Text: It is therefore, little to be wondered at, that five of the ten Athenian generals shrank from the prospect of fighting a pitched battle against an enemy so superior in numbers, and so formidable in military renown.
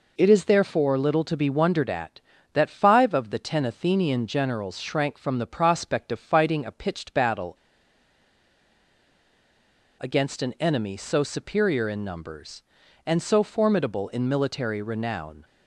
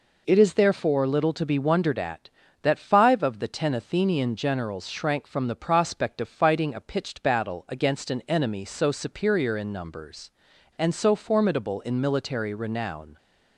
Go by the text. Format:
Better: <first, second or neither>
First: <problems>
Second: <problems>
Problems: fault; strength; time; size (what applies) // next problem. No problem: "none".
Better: second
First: pauses between "battle" and "against"; strong; at 7.5 s; 2.4 s long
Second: none